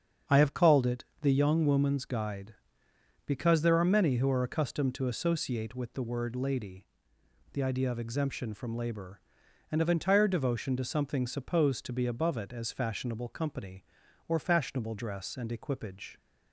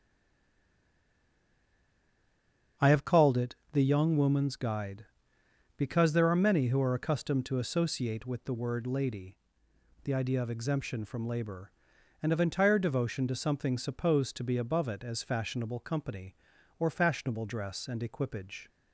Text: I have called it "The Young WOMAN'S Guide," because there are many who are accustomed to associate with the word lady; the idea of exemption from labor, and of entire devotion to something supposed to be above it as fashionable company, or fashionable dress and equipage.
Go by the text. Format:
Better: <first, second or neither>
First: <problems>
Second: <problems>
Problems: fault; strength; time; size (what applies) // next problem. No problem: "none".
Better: first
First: starts louder than the rest; strong; until 1.4 s; 7.5 dB // pauses between "it" and "The"; slight; at 1.0 s; 0.18 s long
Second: stays silent before the first word; strong; until 2.7 s; 2.7 s long // starts louder than the rest; strong; until 3.9 s; 7.5 dB // pauses between "it" and "The"; slight; at 3.5 s; 0.18 s long